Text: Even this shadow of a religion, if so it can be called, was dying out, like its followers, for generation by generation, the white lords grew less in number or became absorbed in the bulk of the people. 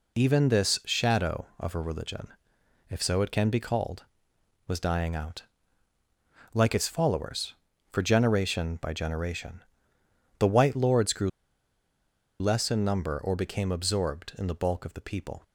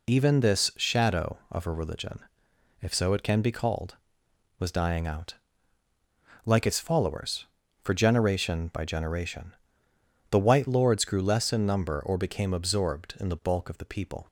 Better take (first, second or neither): second